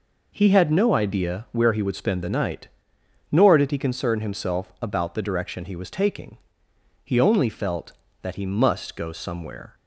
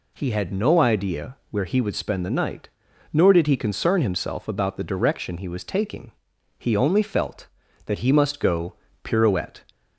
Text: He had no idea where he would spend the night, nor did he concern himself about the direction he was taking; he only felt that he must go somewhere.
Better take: first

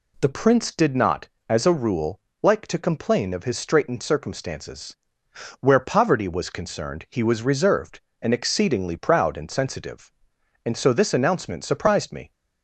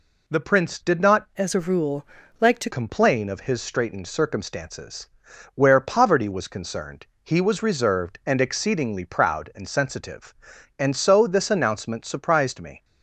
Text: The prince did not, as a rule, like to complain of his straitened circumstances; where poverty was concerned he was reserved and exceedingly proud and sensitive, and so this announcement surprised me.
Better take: first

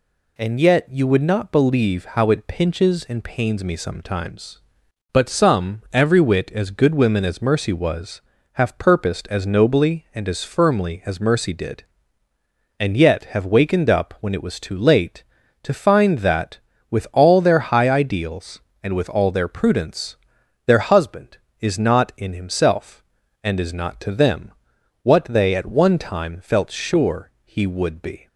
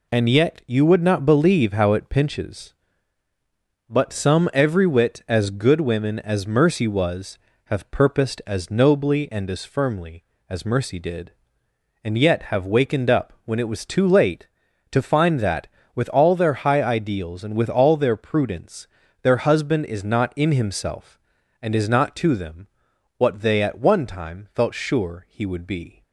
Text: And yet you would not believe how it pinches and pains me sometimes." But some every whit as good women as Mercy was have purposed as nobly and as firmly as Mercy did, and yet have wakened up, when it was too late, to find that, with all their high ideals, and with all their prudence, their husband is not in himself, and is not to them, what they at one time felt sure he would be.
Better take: first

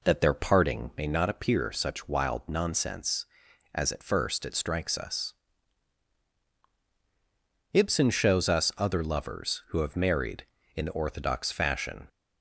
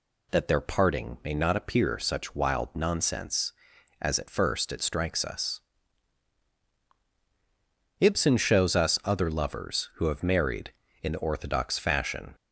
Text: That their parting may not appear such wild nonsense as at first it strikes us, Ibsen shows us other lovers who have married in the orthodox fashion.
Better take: second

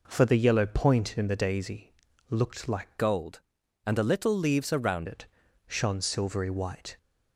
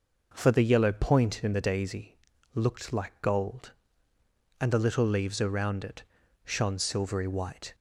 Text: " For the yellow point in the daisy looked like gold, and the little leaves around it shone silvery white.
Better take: second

